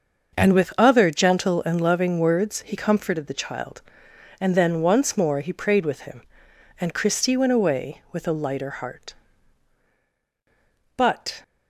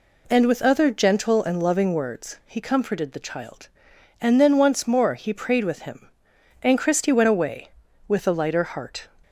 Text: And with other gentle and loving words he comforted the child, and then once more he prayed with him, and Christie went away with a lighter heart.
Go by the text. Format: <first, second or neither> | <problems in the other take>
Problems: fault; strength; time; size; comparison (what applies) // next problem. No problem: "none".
second | starts louder than the rest; until 1.3 s; 6.5 dB // goes on to say "But"; slight; from 10.9 s on; 0.46 s long